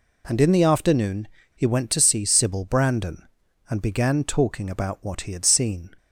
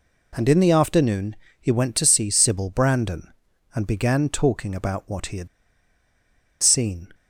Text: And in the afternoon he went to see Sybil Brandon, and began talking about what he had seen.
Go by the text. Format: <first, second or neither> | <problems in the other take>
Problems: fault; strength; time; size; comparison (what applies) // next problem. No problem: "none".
first | pauses between "afternoon" and "he"; slight; at 1.3 s; 0.24 s long; slight in the first // pauses between "had" and "seen"; at 5.4 s; 1.1 s long